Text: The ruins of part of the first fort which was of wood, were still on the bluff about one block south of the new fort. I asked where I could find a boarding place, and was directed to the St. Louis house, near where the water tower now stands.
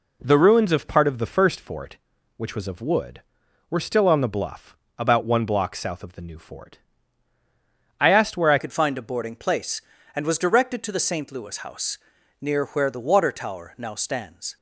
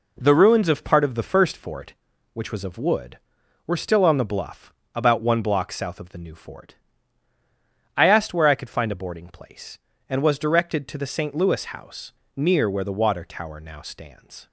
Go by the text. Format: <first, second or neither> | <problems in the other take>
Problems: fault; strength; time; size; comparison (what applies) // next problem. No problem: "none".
second | pauses between "bluff" and "about"; slight; at 4.7 s; 0.22 s long; slight in the second // changes voice at "could"; from 8.5 s on; 6.0 s long